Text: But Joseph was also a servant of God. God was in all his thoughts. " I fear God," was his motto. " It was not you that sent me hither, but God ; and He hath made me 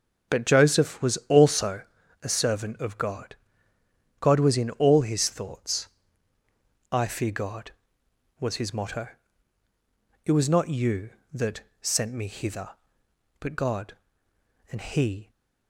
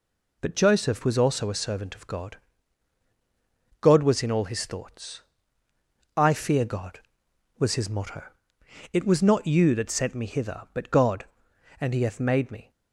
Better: second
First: starts louder than the rest; strong; until 1.4 s; 8 dB // pauses between "also" and "a"; at 1.8 s; 0.40 s long // pauses between "that" and "sent"; slight; at 11.6 s; 0.18 s long // stops before "hath made me"; at 15.3 s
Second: none

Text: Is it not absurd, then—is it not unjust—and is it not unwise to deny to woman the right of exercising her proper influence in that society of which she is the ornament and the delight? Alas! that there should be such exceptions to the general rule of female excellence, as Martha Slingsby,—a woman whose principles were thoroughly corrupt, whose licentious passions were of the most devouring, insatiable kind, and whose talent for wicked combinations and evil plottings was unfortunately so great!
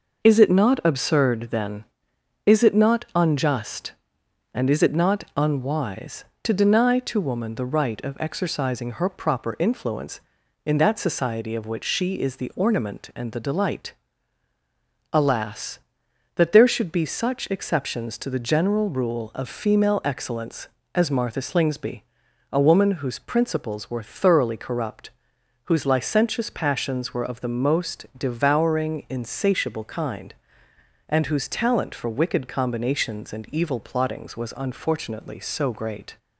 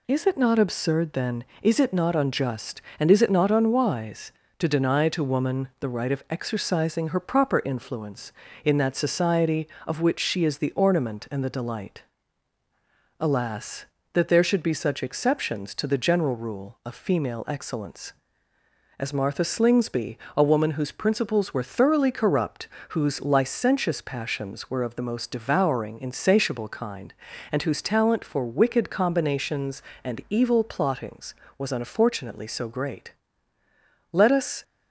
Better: first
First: none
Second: goes on to say "Let us"; from 34.1 s on; 0.50 s long

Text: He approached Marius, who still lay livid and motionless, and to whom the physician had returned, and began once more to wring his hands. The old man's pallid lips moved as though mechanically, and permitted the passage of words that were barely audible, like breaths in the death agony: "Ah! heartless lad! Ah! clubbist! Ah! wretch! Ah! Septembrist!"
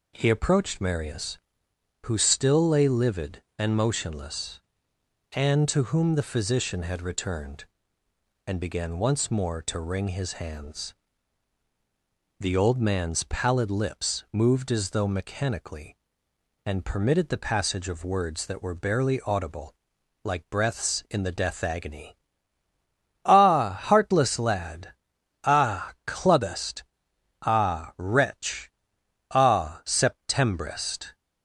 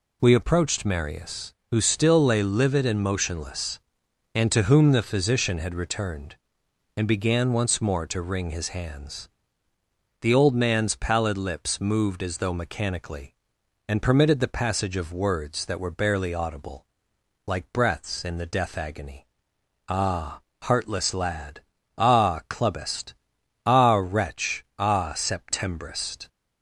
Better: first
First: none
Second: says "We" for "He"; at 0.2 s

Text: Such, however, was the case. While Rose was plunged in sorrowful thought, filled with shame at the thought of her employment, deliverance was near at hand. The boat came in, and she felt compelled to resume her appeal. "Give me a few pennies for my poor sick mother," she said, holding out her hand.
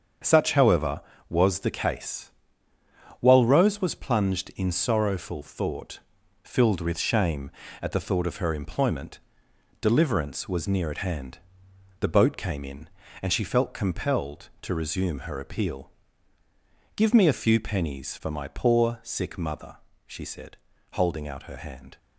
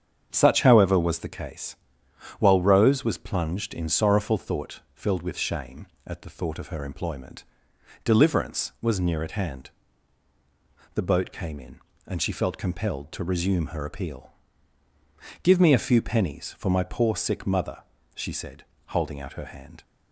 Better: neither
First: starts louder than the rest; strong; until 1.5 s; 7 dB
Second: starts louder than the rest; strong; until 1.3 s; 7.5 dB

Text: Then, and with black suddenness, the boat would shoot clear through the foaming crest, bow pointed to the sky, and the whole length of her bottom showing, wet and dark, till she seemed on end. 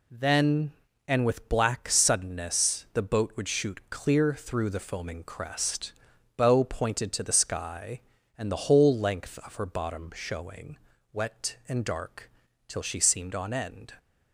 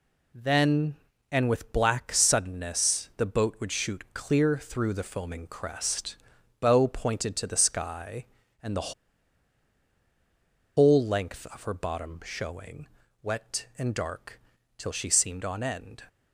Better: first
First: none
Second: pauses between "the" and "whole"; strong; at 8.9 s; 1.8 s long

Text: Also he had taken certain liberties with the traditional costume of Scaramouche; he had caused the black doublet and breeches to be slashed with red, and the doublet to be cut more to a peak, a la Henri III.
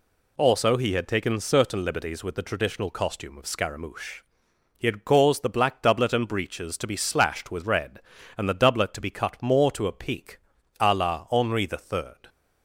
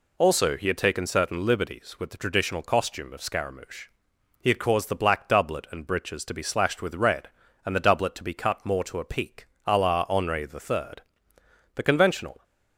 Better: first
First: none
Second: goes on to say "The conventional"; noticeable; from 11.7 s on; 0.68 s long

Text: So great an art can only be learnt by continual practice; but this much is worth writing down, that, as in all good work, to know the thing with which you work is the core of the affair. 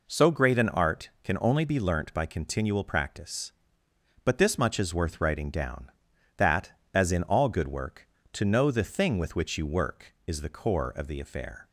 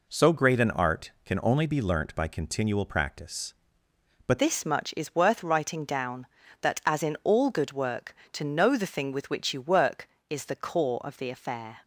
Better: first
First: none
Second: changes voice at "this"; from 4.3 s on; 7.4 s long

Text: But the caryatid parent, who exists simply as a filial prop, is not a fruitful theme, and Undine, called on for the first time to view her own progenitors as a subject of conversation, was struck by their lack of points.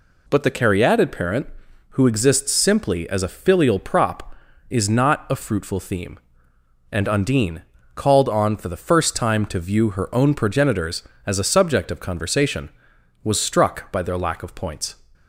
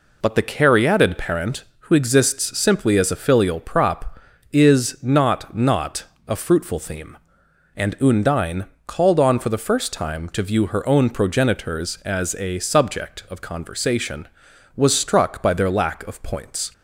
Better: first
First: none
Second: says "not" twice; at 5.5 s

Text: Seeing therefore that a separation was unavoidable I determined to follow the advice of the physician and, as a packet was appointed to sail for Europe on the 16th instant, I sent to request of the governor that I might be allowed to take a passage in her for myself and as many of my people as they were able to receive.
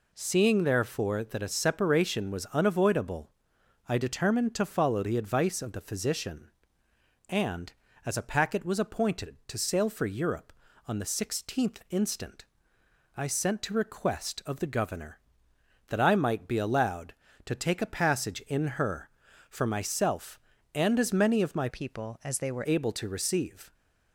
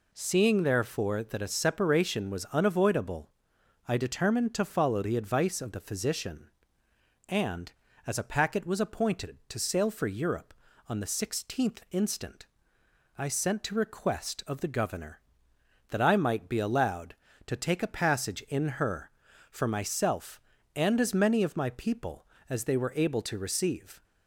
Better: second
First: pauses between "unavoidable" and "I"; noticeable; at 3.3 s; 0.58 s long // changes voice from "people" to "were"; from 21.6 to 22.6 s; 1.0 s long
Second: pauses between "unavoidable" and "I"; noticeable; at 3.2 s; 0.58 s long

